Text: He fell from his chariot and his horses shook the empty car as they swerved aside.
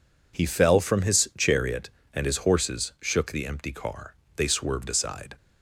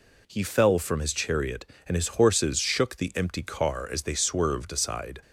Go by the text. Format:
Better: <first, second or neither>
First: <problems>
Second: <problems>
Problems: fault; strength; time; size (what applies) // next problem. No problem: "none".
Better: second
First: skips "as"; at 4.2 s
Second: none